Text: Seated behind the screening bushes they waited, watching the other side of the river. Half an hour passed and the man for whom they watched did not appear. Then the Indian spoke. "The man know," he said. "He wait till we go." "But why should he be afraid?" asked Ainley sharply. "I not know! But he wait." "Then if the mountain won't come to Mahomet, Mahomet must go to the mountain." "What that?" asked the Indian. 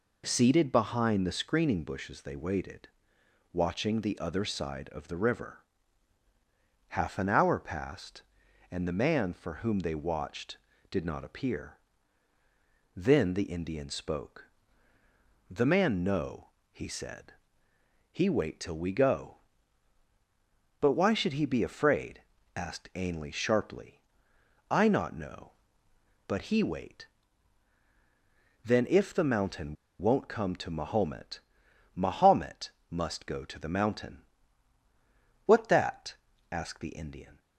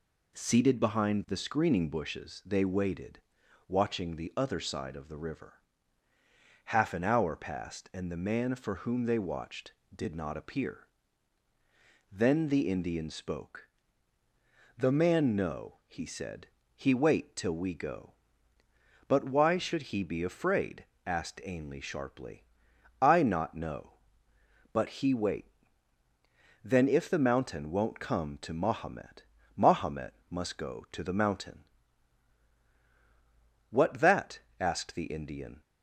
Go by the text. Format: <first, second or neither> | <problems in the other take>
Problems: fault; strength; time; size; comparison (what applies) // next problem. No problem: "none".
second | pauses between "mountain" and "won't"; slight; at 29.7 s; 0.25 s long // pauses between "Mahomet" and "must"; slight; at 32.7 s; 0.18 s long; slight in the second